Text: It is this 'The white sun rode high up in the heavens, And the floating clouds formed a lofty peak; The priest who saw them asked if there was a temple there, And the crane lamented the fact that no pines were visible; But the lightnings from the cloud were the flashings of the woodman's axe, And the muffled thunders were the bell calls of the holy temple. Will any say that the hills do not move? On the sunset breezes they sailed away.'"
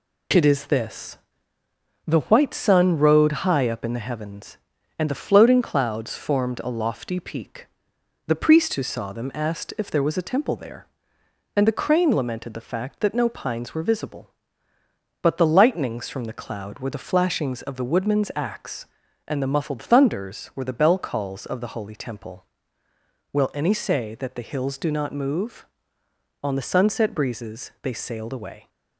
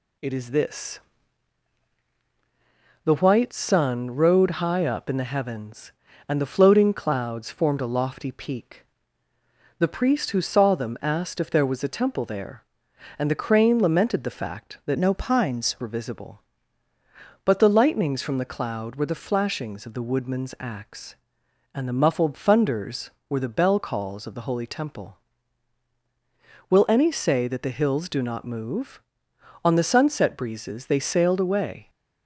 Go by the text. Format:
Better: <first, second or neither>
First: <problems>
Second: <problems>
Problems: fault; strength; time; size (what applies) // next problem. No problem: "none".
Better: first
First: pauses between "this" and "The"; noticeable; at 1.1 s; 0.88 s long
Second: pauses between "this" and "The"; strong; at 0.9 s; 2.0 s long // changes voice from "no" to "pines"; from 14.9 to 15.7 s; 0.8 s long